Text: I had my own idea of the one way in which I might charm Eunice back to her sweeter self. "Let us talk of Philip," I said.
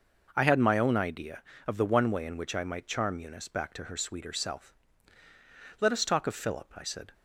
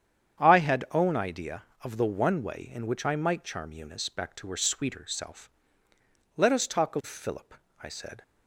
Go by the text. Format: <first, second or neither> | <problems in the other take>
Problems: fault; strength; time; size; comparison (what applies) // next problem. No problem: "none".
first | starts louder than the rest; strong; until 1.4 s; 8.5 dB // skips "my"; at 0.8 s